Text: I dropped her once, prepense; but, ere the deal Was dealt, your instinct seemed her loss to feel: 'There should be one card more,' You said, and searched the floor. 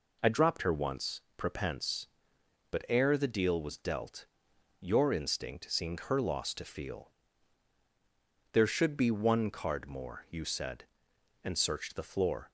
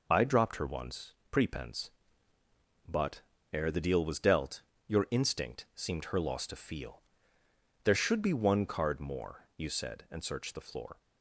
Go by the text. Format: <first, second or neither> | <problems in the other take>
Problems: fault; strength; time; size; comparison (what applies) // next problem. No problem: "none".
neither | none